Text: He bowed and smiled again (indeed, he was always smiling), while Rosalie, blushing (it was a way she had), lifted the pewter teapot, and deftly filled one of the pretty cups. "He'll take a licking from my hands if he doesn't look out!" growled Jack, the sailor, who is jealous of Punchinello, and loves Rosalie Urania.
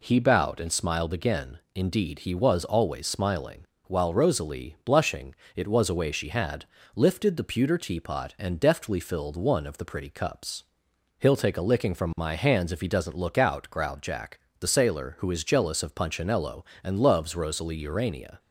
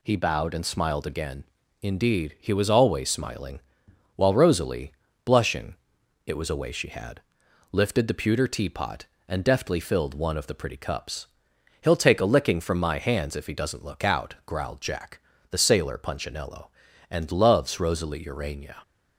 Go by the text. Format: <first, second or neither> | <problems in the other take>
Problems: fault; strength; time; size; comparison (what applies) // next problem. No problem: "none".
first | skips "who is jealous of"; at 15.9 s